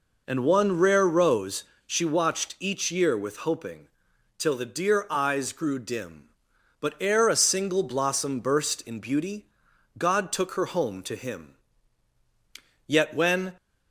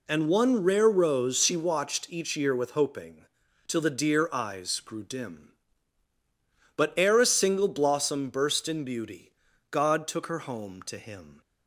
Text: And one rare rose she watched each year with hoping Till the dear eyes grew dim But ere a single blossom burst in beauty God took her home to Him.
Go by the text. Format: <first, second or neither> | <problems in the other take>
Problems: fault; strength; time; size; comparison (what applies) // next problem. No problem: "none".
second | pauses between "rose" and "she"; slight; at 1.6 s; 0.22 s long // pauses between "hoping" and "Till"; noticeable; at 3.8 s; 0.50 s long; also in the second // pauses between "beauty" and "God"; noticeable; at 9.4 s; 0.52 s long; also in the second // goes on to say "Yet when"; noticeable; from 12.8 s on; 0.68 s long